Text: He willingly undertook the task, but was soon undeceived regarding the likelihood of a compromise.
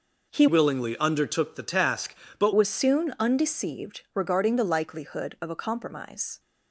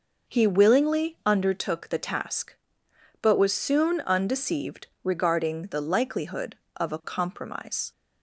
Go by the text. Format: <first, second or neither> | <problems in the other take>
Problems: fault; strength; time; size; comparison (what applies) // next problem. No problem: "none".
second | changes voice from "willingly" to "but"; from 0.4 to 2.5 s; 2.1 s long